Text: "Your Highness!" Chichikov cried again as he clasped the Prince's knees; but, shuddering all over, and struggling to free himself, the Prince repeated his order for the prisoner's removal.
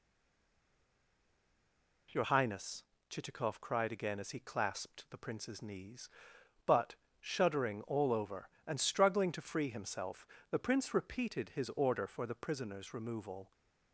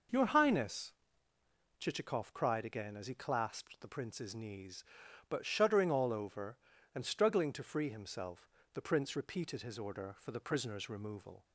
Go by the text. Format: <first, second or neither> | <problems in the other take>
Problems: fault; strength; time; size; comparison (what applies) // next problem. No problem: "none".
second | stays silent before the first word; noticeable; until 2.0 s; 2.0 s long